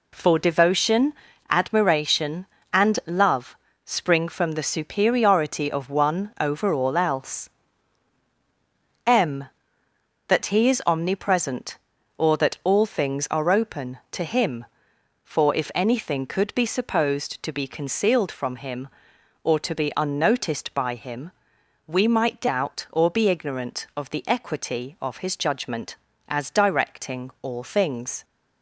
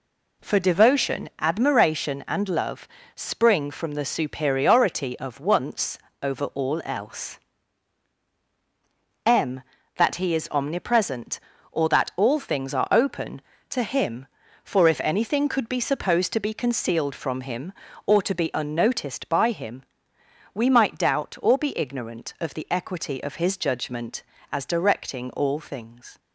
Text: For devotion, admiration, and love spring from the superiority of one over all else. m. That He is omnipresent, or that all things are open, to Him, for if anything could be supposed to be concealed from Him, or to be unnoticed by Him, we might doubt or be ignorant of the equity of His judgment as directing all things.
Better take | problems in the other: first | pauses between "love" and "spring"; slight; at 2.8 s; 0.26 s long; slight in the first // says "once" for "one"; at 5.3 s

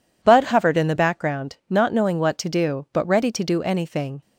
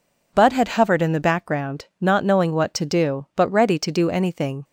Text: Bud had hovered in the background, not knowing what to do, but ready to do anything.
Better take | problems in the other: second | skips "had"; at 0.4 s

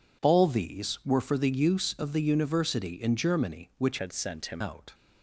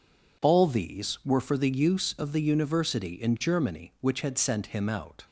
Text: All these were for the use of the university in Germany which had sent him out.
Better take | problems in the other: second | changes voice from "had" to "him"; from 3.9 to 4.6 s; 0.7 s long

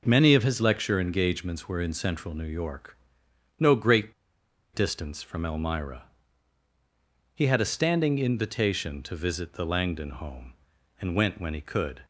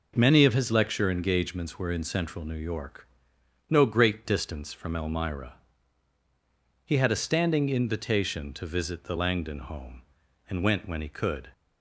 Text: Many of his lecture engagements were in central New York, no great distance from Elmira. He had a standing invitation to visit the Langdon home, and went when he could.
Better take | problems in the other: second | pauses between "great" and "distance"; noticeable; at 4.1 s; 0.60 s long

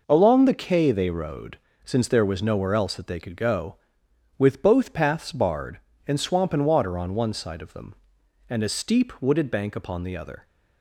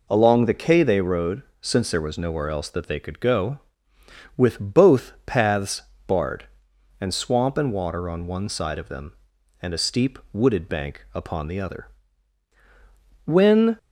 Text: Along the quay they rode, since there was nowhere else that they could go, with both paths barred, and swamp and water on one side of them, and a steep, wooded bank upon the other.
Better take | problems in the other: first | pauses between "paths" and "barred"; slight; at 5.8 s; 0.24 s long // goes on to say "When"; from 13.2 s on; 0.52 s long

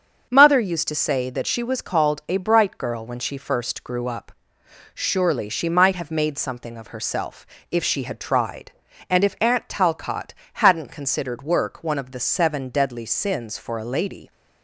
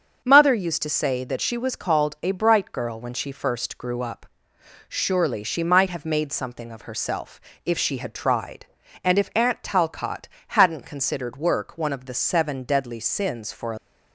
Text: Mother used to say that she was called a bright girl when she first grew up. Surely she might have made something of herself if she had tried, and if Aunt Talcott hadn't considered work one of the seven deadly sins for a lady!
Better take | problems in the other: first | starts louder than the rest; until 1.2 s; 7 dB; also in the first // pauses between "herself" and "if"; slight; at 7.4 s; 0.24 s long; slight in the first // pauses between "Talcott" and "hadn't"; slight; at 10.2 s; 0.20 s long; slight in the first // stops before "lady"; at 13.7 s

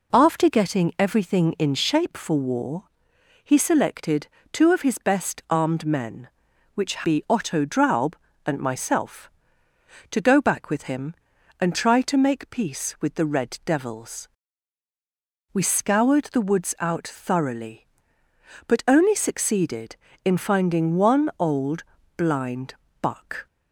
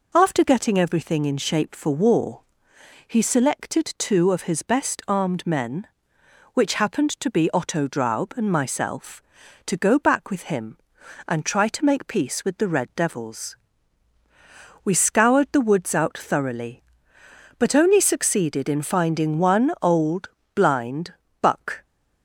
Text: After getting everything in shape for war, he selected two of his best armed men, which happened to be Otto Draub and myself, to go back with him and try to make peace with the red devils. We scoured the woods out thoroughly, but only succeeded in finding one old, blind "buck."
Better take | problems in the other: second | pauses between "selected" and "two"; slight; at 4.2 s; 0.24 s long // skips "happened to"; at 7.0 s // pauses between "blind" and "buck"; slight; at 22.7 s; 0.26 s long; slight in the second

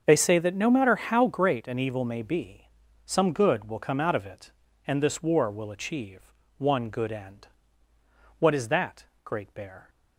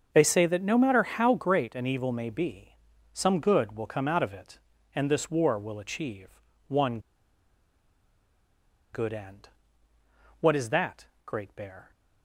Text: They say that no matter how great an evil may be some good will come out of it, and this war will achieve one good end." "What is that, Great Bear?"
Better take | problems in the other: first | starts louder than the rest; until 1.1 s; 6.5 dB; also in the first // pauses between "be" and "some"; at 2.7 s; 0.38 s long; also in the first // pauses between "achieve" and "one"; slight; at 6.4 s; 0.26 s long; slight in the first // pauses between "one" and "good"; strong; at 6.9 s; 1.9 s long

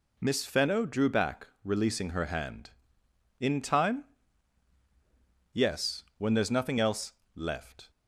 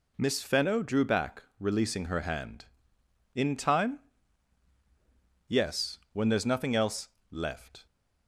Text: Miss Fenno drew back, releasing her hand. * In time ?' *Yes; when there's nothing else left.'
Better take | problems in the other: neither | pauses between "else" and "left"; slight; the same in both

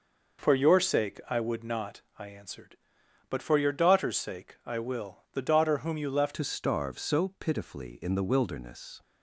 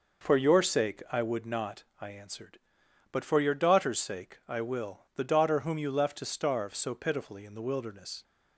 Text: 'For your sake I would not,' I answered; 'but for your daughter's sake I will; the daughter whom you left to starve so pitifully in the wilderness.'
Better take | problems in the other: second | changes voice at "to"; from 6.3 s on; 2.7 s long

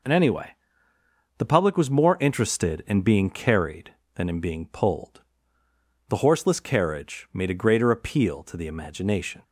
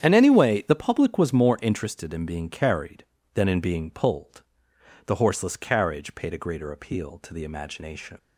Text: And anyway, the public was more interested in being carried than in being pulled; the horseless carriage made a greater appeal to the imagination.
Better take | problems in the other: first | starts louder than the rest; strong; until 1.0 s; 8.5 dB // says "paid" for "made"; at 6.1 s

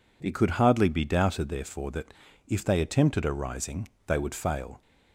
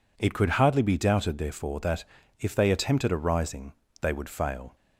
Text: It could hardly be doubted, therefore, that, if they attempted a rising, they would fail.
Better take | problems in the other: neither | none

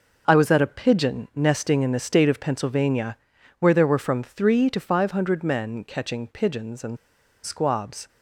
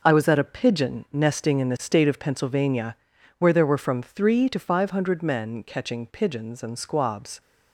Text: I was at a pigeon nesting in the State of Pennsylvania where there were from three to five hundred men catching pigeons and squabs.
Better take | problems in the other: second | pauses between "Pennsylvania" and "where"; at 3.1 s; 0.44 s long; also in the second // pauses between "and" and "squabs"; noticeable; at 6.9 s; 0.48 s long

